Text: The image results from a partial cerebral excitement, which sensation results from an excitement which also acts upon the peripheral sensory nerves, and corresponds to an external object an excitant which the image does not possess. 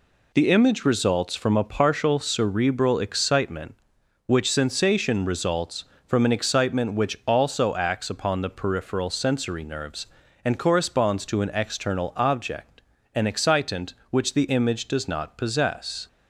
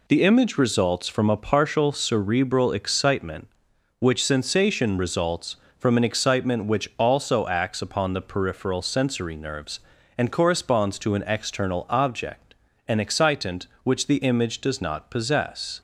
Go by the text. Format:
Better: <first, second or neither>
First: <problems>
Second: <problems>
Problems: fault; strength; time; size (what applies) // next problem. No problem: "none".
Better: neither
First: pauses between "object" and "an"; slight; at 12.8 s; 0.32 s long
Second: pauses between "object" and "an"; slight; at 12.5 s; 0.32 s long